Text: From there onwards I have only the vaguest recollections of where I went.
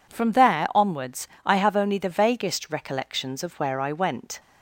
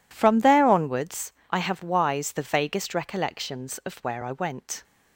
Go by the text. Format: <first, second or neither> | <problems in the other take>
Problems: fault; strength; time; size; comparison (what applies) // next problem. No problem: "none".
first | pauses between "onwards" and "I"; slight; at 1.3 s; 0.18 s long; slight in the first // says "wise" for "only"; at 1.8 s